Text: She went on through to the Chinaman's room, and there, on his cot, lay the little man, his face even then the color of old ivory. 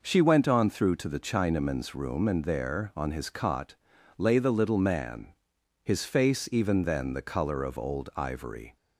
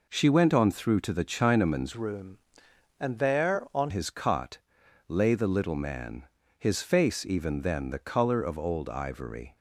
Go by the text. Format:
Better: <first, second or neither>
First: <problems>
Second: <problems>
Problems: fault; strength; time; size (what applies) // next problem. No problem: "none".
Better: first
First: none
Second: changes voice from "room" to "on"; from 1.9 to 3.9 s; 2.0 s long